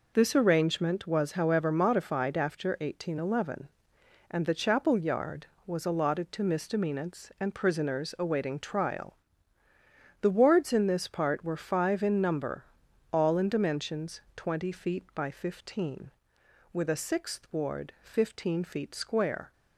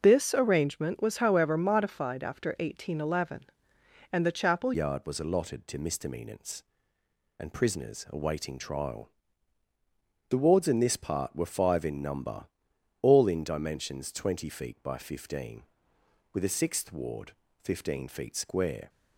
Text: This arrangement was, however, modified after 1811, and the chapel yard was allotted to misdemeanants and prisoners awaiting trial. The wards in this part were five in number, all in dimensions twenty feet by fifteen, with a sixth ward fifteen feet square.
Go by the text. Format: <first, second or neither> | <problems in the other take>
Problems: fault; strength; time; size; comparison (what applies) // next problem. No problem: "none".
first | changes voice at "yard"; from 4.7 s on; 14.1 s long // pauses between "ward" and "fifteen"; slight; at 17.3 s; 0.30 s long